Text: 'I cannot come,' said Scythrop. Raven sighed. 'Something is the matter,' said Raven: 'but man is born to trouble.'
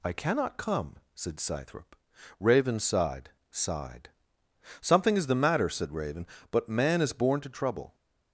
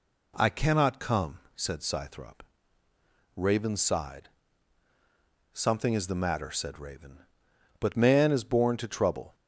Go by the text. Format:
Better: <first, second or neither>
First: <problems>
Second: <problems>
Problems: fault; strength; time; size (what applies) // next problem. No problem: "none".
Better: second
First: says "sighed" twice; at 3.5 s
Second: none